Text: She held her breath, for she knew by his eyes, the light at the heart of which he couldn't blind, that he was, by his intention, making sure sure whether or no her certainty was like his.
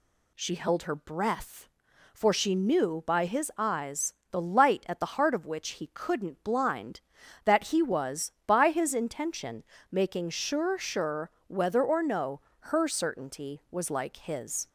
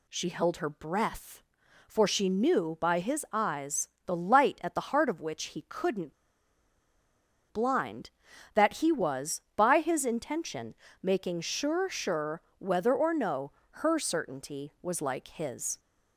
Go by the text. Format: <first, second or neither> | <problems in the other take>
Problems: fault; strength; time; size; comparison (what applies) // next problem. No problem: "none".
first | pauses between "couldn't" and "blind"; strong; at 6.1 s; 1.3 s long // pauses between "sure" and "whether"; slight; at 12.4 s; 0.18 s long; slight in the first // pauses between "no" and "her"; slight; at 13.5 s; 0.26 s long; slight in the first